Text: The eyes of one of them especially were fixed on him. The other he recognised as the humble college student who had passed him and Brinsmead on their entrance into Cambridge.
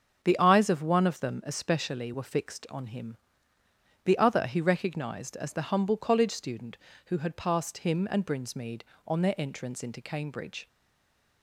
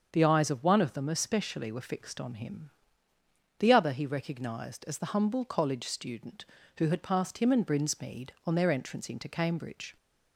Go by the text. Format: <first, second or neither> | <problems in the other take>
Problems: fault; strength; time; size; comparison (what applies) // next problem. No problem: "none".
second | starts louder than the rest; until 1.2 s; 7 dB; also in the second // stays silent after the last word; slight; from 10.6 s on; 0.8 s long